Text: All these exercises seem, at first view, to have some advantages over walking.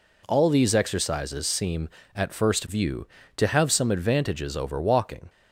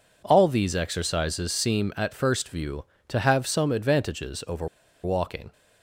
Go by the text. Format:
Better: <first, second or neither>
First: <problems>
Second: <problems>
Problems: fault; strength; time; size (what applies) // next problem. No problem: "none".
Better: first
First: none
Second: pauses between "over" and "walking"; slight; at 4.6 s; 0.35 s long